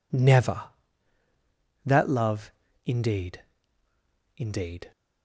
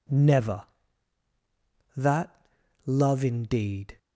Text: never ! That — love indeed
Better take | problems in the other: second | pauses between "love" and "indeed"; slight; at 2.5 s; 0.34 s long // says "indeed" twice; at 4.3 s

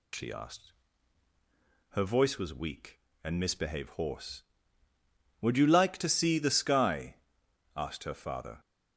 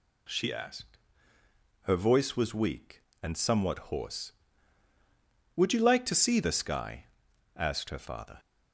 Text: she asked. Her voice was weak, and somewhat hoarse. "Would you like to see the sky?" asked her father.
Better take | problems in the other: second | says "misbehave" for "somewhat"; at 3.3 s

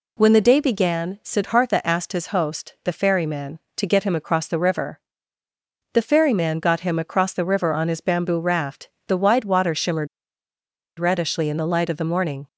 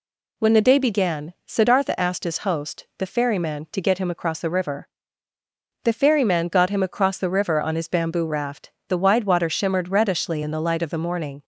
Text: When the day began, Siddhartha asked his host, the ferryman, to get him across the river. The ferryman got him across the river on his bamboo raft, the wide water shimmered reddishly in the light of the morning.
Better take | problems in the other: second | pauses between "shimmered" and "reddishly"; noticeable; at 10.0 s; 0.91 s long

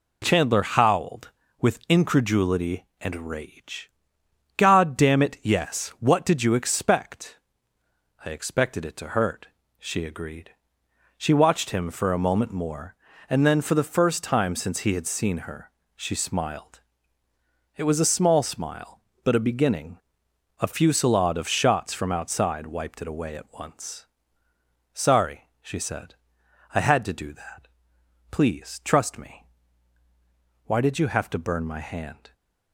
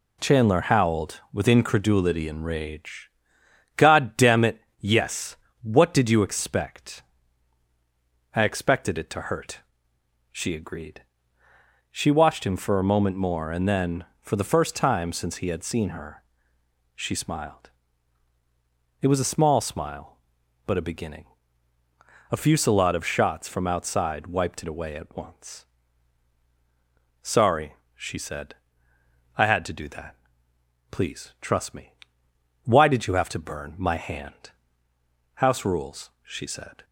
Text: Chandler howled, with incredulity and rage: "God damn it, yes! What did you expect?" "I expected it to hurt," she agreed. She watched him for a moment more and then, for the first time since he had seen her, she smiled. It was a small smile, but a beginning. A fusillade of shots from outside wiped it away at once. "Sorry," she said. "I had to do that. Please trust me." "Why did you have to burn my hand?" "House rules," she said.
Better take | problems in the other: second | stops before "House rules she said"; at 32.3 s

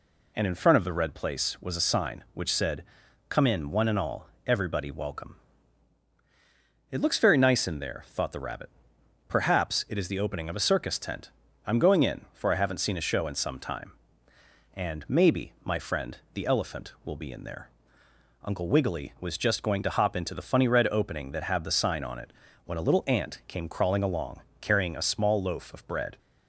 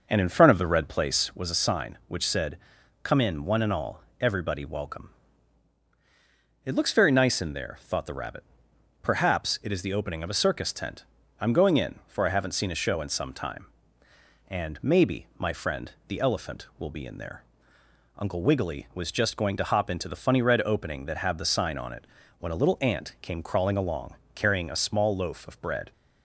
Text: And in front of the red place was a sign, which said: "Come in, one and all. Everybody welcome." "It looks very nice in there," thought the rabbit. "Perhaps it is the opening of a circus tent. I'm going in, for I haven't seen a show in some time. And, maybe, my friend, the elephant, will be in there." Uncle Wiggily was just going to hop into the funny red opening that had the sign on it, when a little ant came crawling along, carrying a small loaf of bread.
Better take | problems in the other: first | starts louder than the rest; noticeable; until 1.4 s; 6 dB

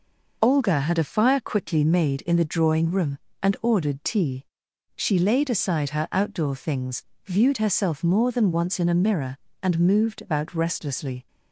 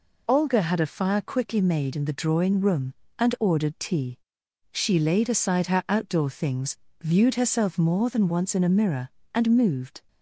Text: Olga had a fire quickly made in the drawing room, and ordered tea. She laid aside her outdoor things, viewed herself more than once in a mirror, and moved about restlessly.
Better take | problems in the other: first | stops before "about restlessly"; at 10.0 s

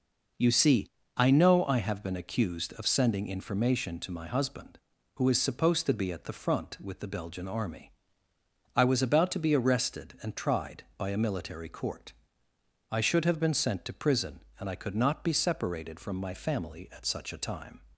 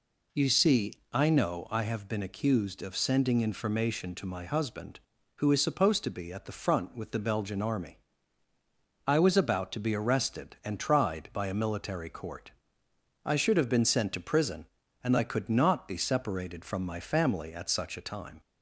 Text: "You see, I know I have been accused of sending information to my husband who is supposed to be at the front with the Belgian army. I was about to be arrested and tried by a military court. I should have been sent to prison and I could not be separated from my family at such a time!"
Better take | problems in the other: neither | none

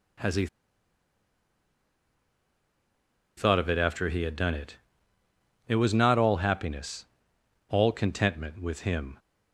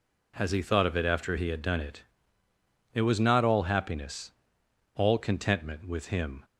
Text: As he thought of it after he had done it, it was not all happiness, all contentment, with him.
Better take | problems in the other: second | pauses between "he" and "thought"; strong; at 0.4 s; 2.9 s long

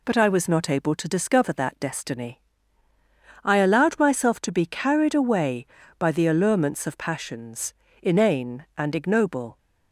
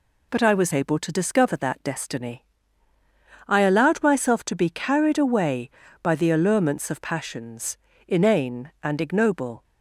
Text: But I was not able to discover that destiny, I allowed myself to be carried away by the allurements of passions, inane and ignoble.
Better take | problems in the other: first | skips "not"; at 0.7 s

